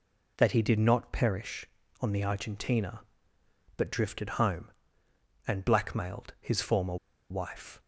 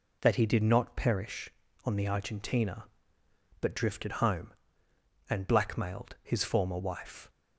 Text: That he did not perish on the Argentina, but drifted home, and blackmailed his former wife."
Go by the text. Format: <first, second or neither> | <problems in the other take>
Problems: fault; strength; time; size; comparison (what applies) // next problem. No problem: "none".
second | pauses between "former" and "wife"; slight; at 6.9 s; 0.34 s long